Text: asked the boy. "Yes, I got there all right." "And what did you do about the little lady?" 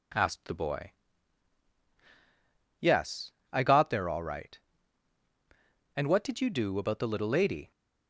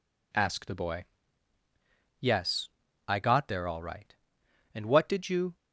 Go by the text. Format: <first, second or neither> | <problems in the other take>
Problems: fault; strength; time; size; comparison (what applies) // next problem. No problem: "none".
first | stops before "do about the little lady"; at 5.5 s